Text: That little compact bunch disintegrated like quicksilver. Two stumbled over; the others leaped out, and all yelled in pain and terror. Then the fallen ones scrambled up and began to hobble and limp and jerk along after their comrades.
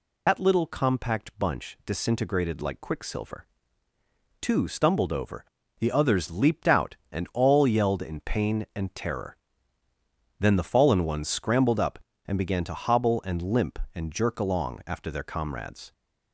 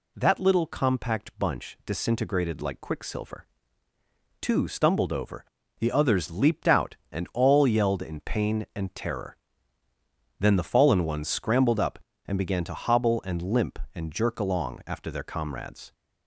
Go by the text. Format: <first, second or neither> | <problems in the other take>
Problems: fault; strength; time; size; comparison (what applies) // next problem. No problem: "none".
second | loses the start of "That"; at 0.2 s; 105 ms